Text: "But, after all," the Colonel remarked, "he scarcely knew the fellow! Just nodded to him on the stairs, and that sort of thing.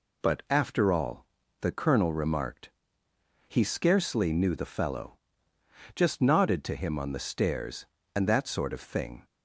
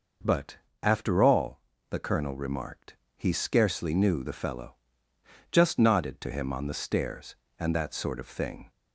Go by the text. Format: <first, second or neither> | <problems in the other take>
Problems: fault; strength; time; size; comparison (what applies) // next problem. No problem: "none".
neither | none